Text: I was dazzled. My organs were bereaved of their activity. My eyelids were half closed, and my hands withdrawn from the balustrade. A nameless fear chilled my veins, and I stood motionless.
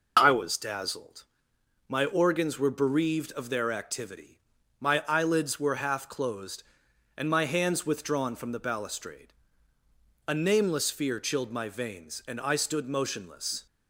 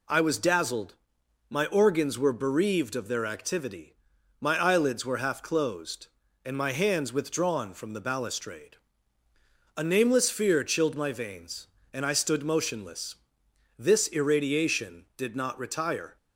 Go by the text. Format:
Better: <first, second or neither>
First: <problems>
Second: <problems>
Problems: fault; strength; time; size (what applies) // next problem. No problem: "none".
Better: first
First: none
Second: goes on to say "This irradiation did not retire"; strong; from 13.7 s on; 2.3 s long